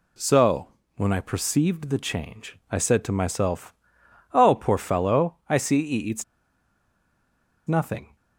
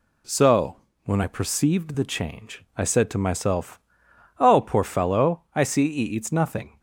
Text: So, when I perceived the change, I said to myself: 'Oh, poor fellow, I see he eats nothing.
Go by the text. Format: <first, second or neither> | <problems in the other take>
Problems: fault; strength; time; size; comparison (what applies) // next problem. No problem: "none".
second | pauses between "eats" and "nothing"; strong; at 6.2 s; 1.4 s long